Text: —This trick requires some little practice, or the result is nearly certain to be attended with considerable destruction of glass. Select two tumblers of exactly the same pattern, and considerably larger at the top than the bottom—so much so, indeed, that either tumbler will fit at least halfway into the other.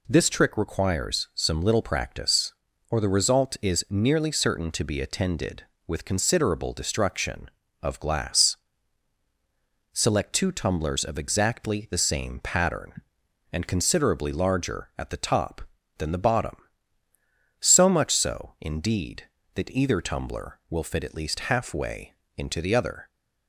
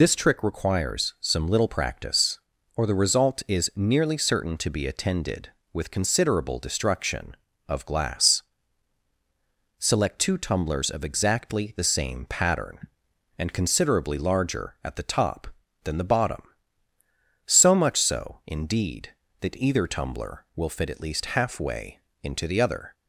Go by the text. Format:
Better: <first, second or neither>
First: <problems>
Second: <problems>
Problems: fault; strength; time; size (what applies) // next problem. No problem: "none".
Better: first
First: pauses between "halfway" and "into"; slight; at 22.1 s; 0.24 s long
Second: loses the start of "This"; at 0.0 s; 85 ms // pauses between "halfway" and "into"; slight; at 21.9 s; 0.24 s long